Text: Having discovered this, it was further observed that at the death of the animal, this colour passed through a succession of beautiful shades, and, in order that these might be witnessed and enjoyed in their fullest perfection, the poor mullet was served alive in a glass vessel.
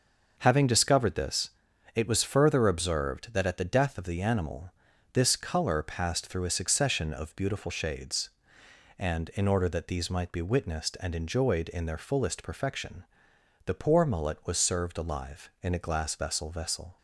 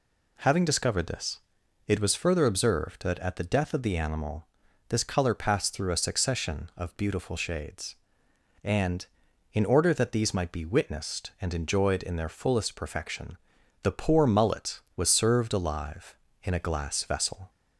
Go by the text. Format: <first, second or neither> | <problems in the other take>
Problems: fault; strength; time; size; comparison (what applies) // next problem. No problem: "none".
second | starts louder than the rest; until 1.3 s; 6.5 dB // says "vessel" twice; at 16.5 s